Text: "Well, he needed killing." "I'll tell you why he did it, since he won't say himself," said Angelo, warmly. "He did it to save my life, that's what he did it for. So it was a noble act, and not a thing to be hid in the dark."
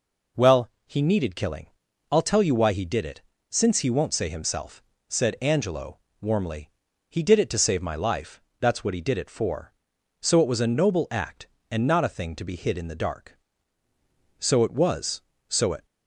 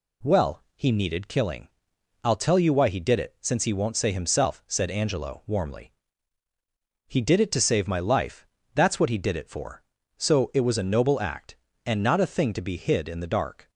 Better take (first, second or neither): second